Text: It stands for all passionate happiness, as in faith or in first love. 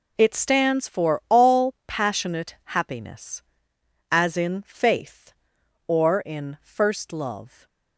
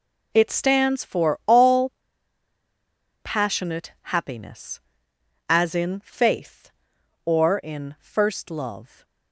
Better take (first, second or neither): first